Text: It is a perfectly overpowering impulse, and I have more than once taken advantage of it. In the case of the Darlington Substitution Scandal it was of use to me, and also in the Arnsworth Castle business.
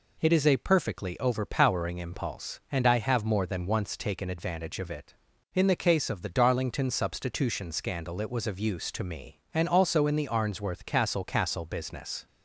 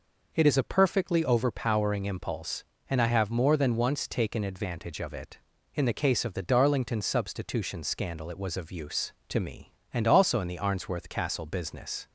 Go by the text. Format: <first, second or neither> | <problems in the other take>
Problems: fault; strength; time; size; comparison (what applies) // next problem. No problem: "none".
second | says "Castle" twice; at 11.2 s